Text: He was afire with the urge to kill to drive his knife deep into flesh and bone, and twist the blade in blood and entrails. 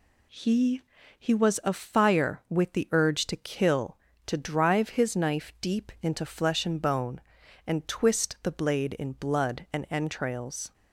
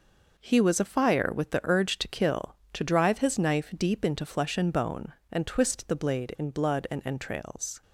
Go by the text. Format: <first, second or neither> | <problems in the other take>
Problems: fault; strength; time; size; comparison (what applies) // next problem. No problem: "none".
second | says "He" twice; at 1.1 s